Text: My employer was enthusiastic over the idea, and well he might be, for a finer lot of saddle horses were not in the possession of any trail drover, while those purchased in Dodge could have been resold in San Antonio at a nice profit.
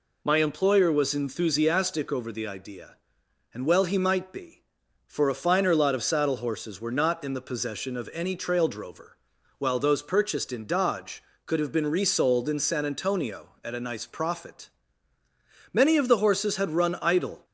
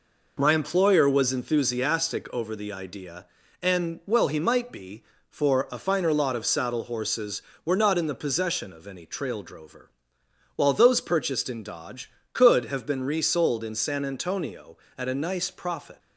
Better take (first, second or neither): second